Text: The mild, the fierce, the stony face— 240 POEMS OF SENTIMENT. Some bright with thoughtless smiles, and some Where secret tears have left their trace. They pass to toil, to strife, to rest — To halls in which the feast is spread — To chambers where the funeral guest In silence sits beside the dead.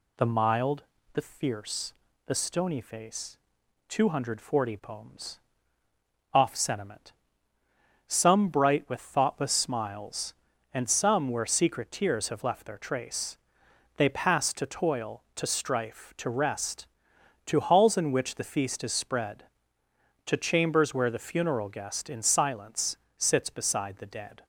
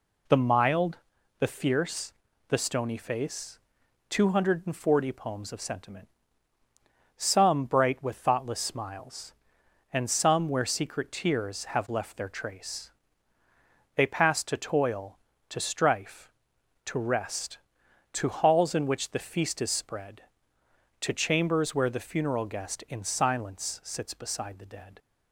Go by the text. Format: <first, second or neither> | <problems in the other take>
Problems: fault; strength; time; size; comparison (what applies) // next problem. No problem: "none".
second | says "Off" for "OF"; at 6.3 s // pauses between "silence" and "sits"; slight; at 22.9 s; 0.22 s long